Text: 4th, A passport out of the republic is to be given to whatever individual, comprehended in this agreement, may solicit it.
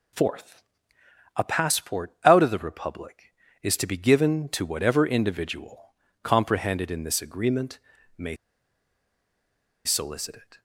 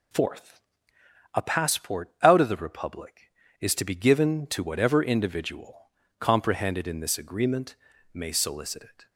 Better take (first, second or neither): second